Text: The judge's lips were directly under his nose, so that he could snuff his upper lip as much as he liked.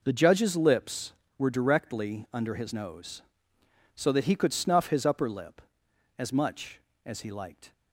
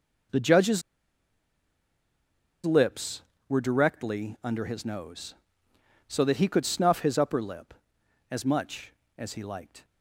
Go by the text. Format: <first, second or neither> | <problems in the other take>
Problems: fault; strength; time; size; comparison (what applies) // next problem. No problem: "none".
first | pauses between "judge's" and "lips"; strong; at 0.8 s; 1.8 s long